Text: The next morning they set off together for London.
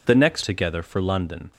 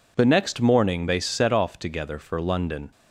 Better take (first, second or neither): second